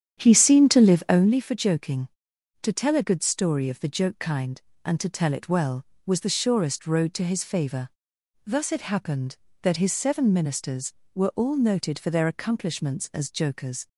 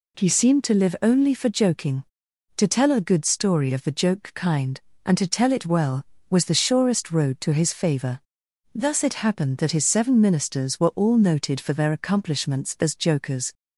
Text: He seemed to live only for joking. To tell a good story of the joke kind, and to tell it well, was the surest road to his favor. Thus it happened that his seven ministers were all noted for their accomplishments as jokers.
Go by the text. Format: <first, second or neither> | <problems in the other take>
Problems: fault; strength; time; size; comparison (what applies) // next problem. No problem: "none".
second | starts louder than the rest; strong; until 1.4 s; 9 dB